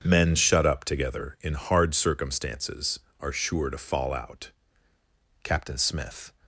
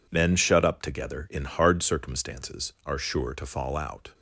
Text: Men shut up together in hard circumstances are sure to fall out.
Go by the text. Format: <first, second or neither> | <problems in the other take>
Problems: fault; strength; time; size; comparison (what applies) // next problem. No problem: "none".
second | starts louder than the rest; until 1.0 s; 6.5 dB // goes on to say "Captain Smith"; noticeable; from 5.4 s on; 0.88 s long